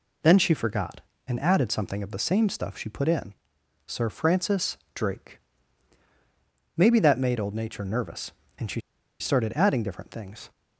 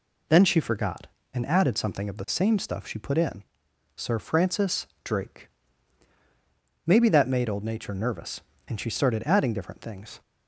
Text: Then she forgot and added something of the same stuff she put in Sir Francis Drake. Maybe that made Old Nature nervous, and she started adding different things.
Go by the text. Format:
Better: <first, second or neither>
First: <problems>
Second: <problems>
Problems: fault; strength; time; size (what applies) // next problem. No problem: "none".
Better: second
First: pauses between "in" and "Sir"; noticeable; at 3.3 s; 0.52 s long // pauses between "Francis" and "Drake"; slight; at 4.7 s; 0.18 s long // pauses between "she" and "started"; at 8.7 s; 0.41 s long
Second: pauses between "in" and "Sir"; noticeable; at 3.4 s; 0.52 s long // pauses between "Francis" and "Drake"; slight; at 4.8 s; 0.18 s long